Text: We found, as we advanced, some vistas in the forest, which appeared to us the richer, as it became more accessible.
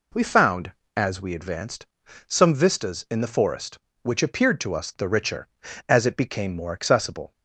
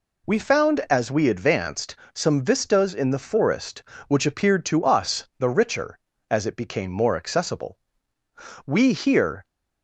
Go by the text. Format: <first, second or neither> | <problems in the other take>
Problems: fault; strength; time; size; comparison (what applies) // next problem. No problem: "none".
first | goes on to say "We here"; noticeable; from 8.6 s on; 0.80 s long